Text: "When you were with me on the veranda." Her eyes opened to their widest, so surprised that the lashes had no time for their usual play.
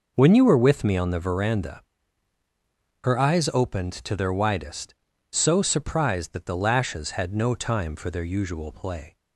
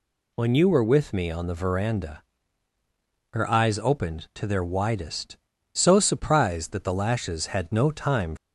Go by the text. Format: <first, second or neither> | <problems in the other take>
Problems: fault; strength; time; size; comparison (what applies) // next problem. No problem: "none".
first | stops before "for their usual play"; at 8.3 s